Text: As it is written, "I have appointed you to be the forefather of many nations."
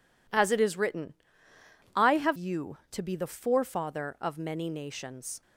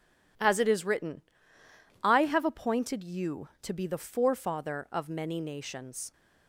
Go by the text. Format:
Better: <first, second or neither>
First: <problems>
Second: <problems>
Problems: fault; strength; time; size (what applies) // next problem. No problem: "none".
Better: second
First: skips "appointed"; at 2.3 s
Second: none